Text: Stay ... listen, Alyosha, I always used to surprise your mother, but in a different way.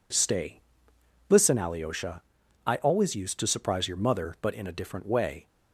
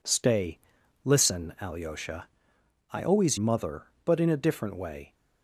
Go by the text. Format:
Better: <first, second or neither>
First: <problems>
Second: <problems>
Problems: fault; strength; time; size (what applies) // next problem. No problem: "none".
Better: first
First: none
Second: skips "used to surprise your"; at 3.3 s